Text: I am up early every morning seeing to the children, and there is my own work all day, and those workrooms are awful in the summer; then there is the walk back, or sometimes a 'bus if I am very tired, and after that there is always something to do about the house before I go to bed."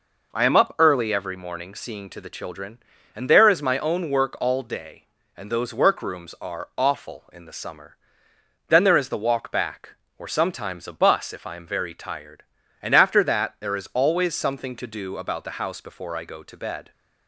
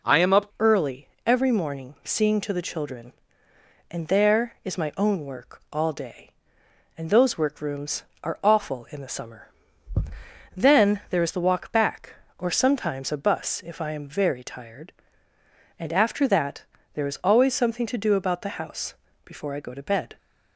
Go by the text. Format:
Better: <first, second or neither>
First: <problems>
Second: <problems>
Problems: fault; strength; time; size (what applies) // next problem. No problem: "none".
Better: first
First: none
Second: changes voice at "early"; from 0.5 s on; 19.6 s long // pauses between "early" and "every"; slight; at 1.0 s; 0.18 s long // pauses between "that" and "there"; slight; at 16.6 s; 0.30 s long // pauses between "house" and "before"; slight; at 18.9 s; 0.30 s long